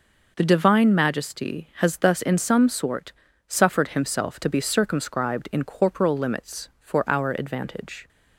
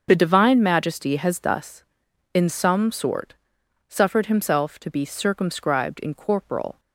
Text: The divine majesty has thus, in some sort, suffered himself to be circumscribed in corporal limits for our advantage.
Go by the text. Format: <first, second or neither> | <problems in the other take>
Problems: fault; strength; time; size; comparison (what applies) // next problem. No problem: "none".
first | starts louder than the rest; until 1.1 s; 6.5 dB // stops before "limits for our advantage"; at 6.7 s